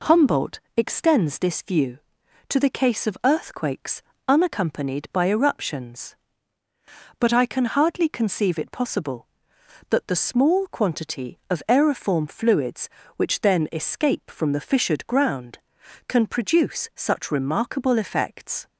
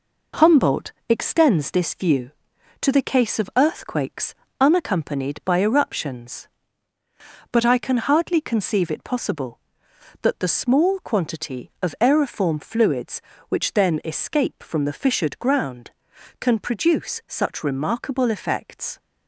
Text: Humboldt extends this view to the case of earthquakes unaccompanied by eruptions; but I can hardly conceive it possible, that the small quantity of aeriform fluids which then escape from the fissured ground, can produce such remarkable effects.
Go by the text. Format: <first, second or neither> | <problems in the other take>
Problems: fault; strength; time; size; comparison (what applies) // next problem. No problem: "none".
first | gets quieter; noticeable; throughout; 4.5 dB // pauses between "Humboldt" and "extends"; slight; at 0.9 s; 0.18 s long; slight in the first // pauses between "earthquakes" and "unaccompanied"; slight; at 4.3 s; 0.24 s long; slight in the first